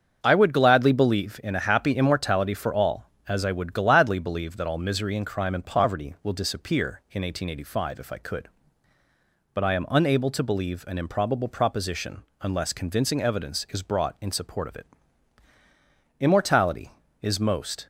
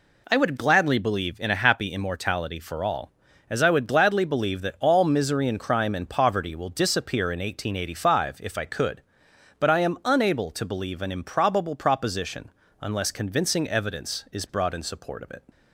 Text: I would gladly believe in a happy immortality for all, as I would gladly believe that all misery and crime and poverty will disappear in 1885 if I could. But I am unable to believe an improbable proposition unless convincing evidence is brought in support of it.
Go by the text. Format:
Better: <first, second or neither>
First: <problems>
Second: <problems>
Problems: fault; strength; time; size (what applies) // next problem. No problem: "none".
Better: second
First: starts louder than the rest; until 1.2 s; 7 dB // pauses between "proposition" and "unless"; slight; at 12.2 s; 0.20 s long // goes on to say "Immortality is most"; strong; from 16.1 s on; 1.6 s long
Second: pauses between "proposition" and "unless"; slight; at 12.5 s; 0.30 s long